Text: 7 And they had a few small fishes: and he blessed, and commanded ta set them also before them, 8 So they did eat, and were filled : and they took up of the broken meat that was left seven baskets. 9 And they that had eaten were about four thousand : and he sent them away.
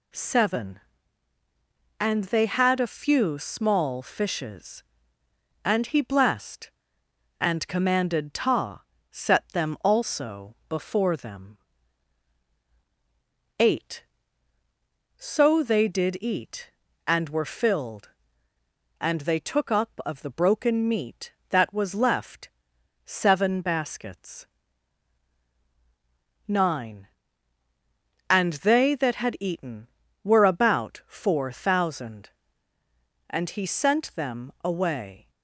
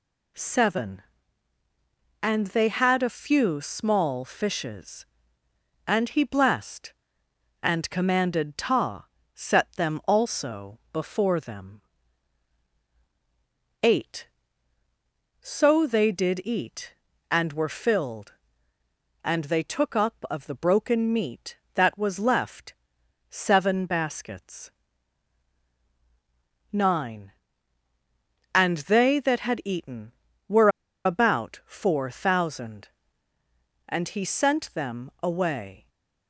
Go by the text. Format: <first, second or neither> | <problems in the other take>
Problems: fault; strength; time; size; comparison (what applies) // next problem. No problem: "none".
first | pauses between "ta" and "set"; slight; at 9.0 s; 0.28 s long; slight in the first // pauses between "left" and "seven"; noticeable; at 22.7 s; 0.56 s long; noticeable in the first // pauses between "were" and "about"; at 30.6 s; 0.37 s long